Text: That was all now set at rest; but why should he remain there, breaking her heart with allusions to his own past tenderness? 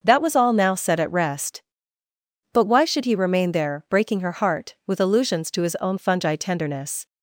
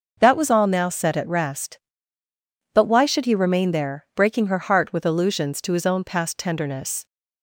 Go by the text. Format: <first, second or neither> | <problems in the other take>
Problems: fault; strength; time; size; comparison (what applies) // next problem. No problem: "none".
second | starts louder than the rest; until 1.0 s; 6.5 dB; noticeable in the second // says "fungi" for "past"; at 5.9 s